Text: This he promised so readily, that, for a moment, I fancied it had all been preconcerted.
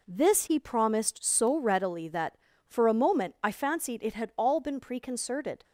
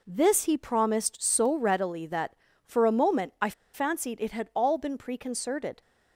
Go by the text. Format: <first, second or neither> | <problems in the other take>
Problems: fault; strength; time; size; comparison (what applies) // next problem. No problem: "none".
first | pauses between "I" and "fancied"; slight; at 3.5 s; 0.22 s long